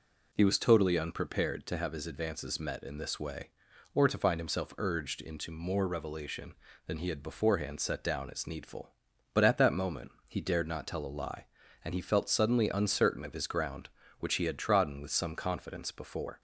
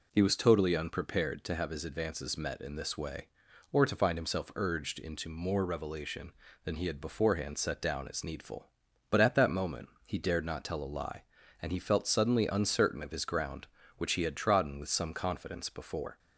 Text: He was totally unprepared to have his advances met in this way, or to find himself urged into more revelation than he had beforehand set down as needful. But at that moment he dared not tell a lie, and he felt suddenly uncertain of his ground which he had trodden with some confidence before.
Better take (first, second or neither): neither